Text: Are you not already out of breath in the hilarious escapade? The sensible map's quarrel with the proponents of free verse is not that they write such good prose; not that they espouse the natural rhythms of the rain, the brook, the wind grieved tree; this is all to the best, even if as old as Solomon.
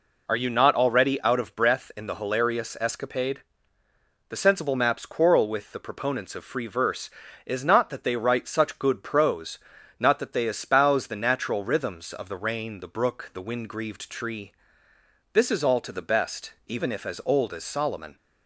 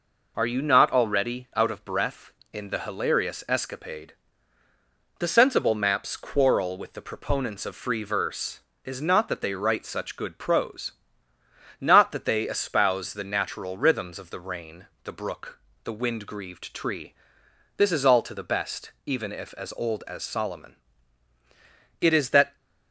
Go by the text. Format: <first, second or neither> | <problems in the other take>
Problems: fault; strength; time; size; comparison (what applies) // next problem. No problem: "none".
first | goes on to say "It is that"; from 22.0 s on; 0.54 s long